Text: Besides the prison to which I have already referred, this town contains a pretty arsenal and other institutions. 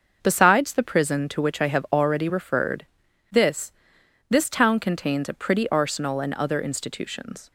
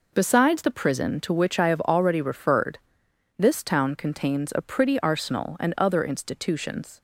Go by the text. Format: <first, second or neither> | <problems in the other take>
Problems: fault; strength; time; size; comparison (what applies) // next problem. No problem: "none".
second | starts louder than the rest; until 1.2 s; 6.5 dB // says "this" twice; at 4.2 s